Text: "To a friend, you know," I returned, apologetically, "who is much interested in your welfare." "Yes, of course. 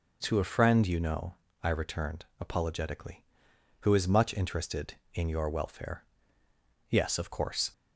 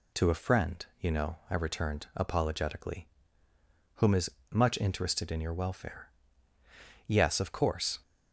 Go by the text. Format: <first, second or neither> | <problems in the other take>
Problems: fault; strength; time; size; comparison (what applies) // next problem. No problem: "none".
first | says "whom" for "who"; at 3.9 s // pauses between "is" and "much"; slight; at 4.3 s; 0.18 s long